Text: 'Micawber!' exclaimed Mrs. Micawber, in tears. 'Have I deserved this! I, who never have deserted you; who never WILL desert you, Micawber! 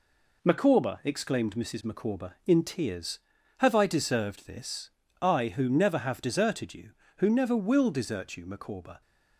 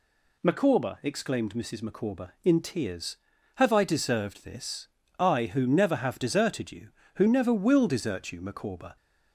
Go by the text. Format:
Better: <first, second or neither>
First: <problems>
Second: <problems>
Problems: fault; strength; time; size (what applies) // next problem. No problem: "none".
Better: second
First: gets quieter; noticeable; throughout; 4.5 dB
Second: none